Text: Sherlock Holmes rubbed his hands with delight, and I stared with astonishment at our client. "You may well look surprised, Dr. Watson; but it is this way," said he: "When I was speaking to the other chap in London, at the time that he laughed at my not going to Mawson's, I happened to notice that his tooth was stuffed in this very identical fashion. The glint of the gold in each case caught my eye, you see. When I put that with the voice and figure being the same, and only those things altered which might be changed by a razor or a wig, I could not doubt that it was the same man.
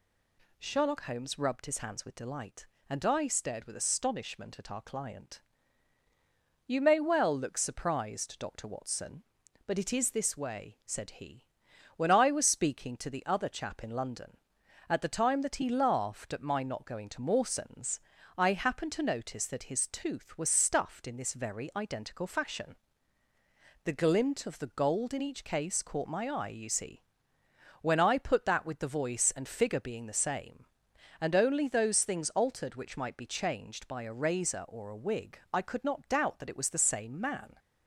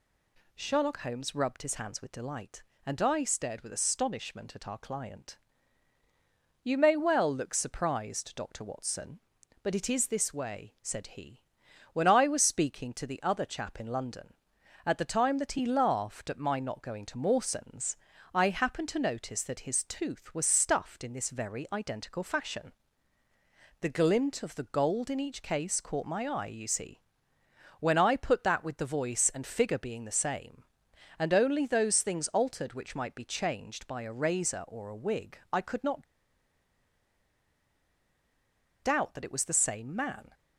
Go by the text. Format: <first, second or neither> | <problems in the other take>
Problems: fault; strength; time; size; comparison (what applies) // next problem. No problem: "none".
first | pauses between "not" and "doubt"; strong; at 36.0 s; 2.7 s long